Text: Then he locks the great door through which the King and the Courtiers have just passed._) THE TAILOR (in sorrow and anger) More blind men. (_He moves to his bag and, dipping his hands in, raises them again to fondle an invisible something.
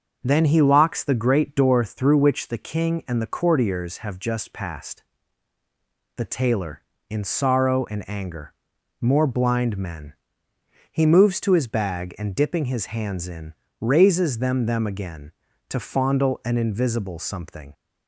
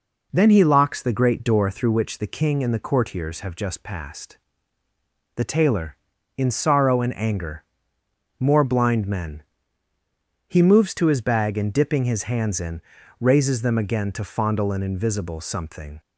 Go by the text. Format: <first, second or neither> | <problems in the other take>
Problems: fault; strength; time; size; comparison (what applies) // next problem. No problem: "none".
second | starts louder than the rest; until 1.2 s; 6.5 dB // says "them" twice; at 14.6 s